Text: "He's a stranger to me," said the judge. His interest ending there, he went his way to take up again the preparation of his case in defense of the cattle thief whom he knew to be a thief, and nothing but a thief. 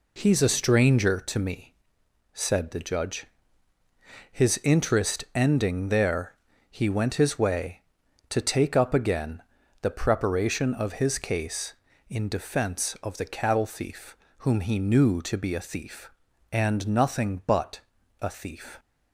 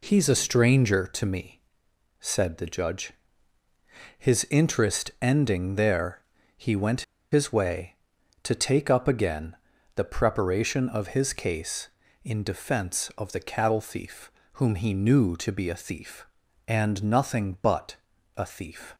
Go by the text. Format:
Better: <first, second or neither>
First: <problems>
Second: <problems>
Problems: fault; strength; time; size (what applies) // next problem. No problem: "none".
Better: first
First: pauses between "again" and "the"; at 9.4 s; 0.40 s long // pauses between "thief" and "whom"; slight; at 14.1 s; 0.22 s long // pauses between "but" and "a"; at 17.8 s; 0.40 s long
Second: pauses between "went" and "his"; slight; at 7.0 s; 0.30 s long // pauses between "again" and "the"; at 9.5 s; 0.40 s long // pauses between "thief" and "whom"; slight; at 14.3 s; 0.22 s long // pauses between "but" and "a"; at 17.9 s; 0.40 s long